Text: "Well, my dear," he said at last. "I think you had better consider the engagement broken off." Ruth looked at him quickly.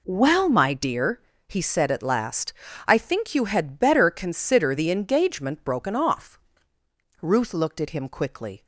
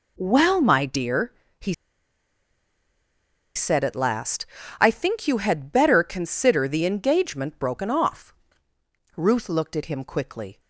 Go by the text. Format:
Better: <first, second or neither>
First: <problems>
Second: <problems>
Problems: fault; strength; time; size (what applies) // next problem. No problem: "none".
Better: first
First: none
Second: pauses between "he" and "said"; strong; at 1.7 s; 1.8 s long